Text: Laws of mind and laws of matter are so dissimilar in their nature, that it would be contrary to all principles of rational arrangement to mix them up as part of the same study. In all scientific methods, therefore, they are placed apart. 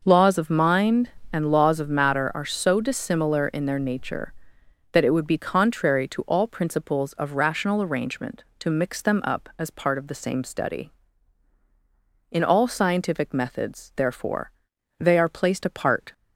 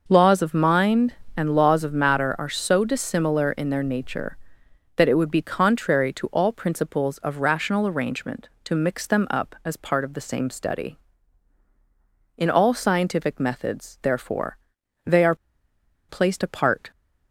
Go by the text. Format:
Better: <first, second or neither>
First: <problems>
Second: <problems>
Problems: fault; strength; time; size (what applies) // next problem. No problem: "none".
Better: first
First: none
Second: pauses between "are" and "placed"; noticeable; at 15.3 s; 0.73 s long